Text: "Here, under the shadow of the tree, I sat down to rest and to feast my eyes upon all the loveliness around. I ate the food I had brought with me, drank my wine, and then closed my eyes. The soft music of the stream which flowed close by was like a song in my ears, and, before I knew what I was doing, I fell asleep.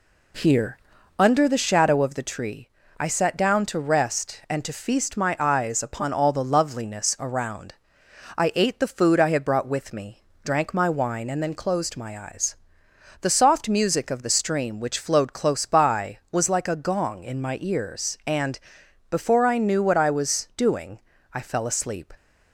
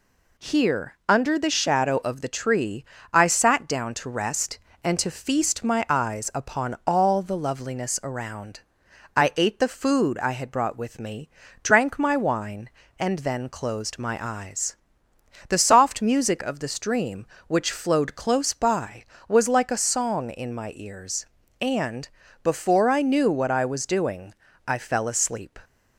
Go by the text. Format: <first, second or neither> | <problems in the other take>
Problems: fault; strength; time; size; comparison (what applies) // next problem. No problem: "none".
second | says "gong" for "song"; at 16.7 s